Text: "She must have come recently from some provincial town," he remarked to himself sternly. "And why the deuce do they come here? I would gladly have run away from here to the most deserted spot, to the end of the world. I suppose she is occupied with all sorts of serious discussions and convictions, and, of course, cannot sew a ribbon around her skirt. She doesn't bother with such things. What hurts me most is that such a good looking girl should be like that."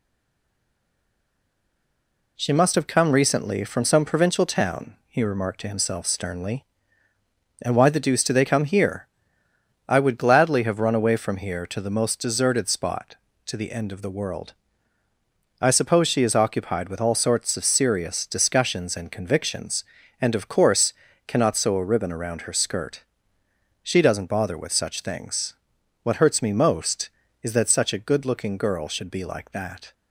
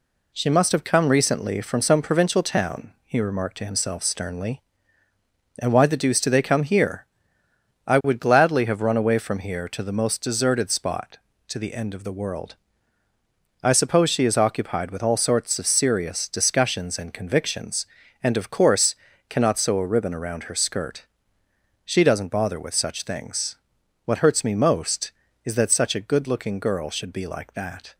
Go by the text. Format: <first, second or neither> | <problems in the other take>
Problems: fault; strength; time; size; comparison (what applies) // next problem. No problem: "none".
second | stays silent before the first word; until 2.3 s; 2.3 s long